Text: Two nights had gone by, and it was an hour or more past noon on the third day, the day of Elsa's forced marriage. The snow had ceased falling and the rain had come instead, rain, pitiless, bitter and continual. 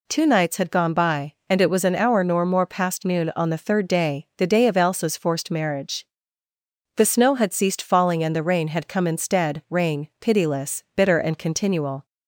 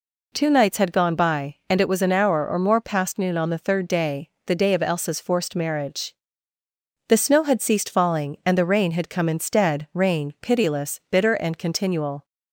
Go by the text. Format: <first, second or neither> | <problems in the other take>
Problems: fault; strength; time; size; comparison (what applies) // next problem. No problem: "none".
second | says "nor" for "or"; at 2.2 s